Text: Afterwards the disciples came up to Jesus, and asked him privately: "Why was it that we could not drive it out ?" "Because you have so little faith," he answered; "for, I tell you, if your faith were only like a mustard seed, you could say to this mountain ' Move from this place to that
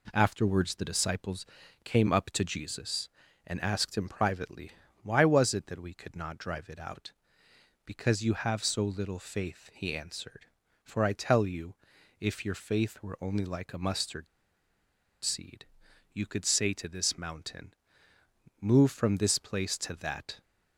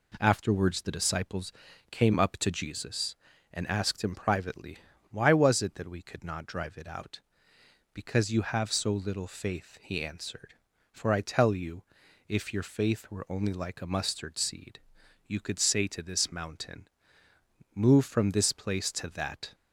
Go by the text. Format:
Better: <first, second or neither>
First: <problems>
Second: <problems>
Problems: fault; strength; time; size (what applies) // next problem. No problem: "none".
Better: second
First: pauses between "disciples" and "came"; at 1.4 s; 0.38 s long // pauses between "mustard" and "seed"; noticeable; at 14.2 s; 0.96 s long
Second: pauses between "disciples" and "came"; at 1.5 s; 0.38 s long